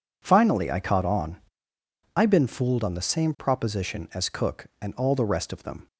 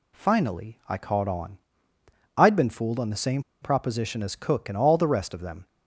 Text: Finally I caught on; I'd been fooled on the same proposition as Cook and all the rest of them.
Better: first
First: none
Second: pauses between "same" and "proposition"; slight; at 3.4 s; 0.19 s long

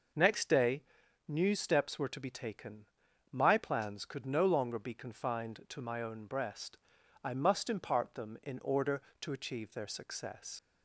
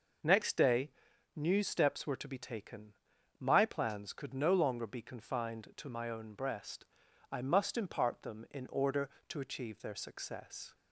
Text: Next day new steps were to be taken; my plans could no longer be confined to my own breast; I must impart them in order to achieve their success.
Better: second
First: pauses between "day" and "new"; noticeable; at 0.8 s; 0.46 s long // leaves "success" unfinished; at 10.5 s; 80 ms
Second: pauses between "day" and "new"; noticeable; at 0.9 s; 0.46 s long

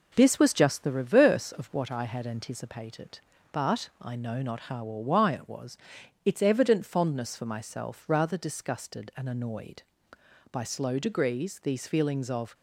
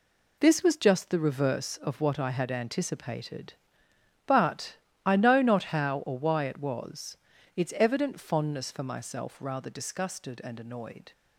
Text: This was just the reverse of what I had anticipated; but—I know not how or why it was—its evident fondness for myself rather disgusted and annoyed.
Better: second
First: goes on to say "By slow degrees these feelings of"; strong; from 10.5 s on; 2.0 s long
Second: none

